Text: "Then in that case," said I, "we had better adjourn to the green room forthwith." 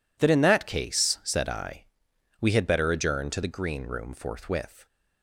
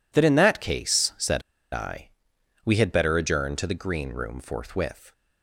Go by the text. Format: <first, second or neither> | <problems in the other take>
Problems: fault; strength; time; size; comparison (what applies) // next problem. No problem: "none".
first | pauses between "said" and "I"; slight; at 1.4 s; 0.32 s long